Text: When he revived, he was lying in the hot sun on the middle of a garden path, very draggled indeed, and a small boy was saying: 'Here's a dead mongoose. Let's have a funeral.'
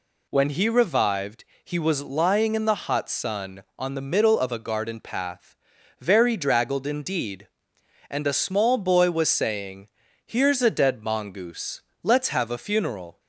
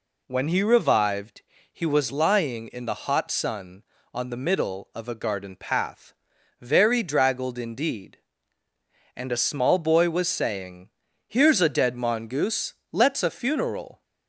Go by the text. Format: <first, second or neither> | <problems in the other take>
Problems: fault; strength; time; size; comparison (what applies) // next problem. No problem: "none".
first | skips "have"; at 13.2 s